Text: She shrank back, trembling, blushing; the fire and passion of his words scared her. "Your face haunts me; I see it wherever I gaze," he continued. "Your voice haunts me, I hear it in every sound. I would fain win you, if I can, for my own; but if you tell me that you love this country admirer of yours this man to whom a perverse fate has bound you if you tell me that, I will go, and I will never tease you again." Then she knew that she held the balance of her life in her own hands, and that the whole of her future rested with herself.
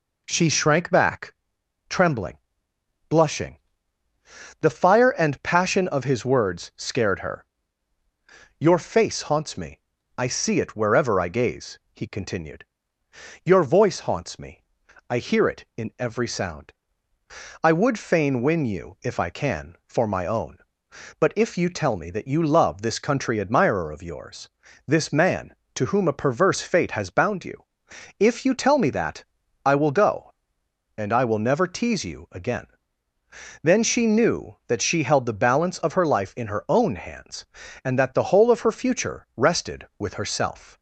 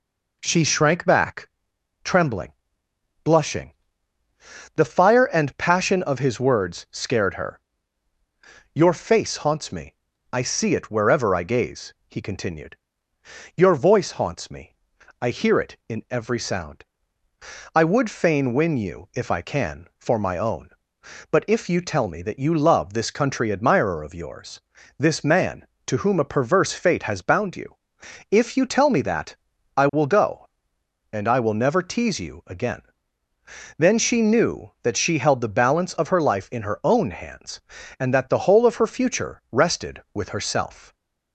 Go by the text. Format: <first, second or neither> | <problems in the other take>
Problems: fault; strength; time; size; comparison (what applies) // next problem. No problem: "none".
neither | pauses between "yours" and "this"; the same in both // pauses between "you" and "if"; noticeable; the same in both